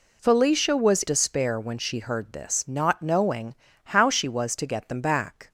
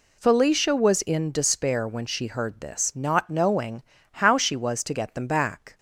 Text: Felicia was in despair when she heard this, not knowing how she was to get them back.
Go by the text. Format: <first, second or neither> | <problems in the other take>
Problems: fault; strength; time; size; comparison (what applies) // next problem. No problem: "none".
second | skips "in"; at 1.0 s // pauses between "knowing" and "how"; slight; at 3.5 s; 0.32 s long; slight in the second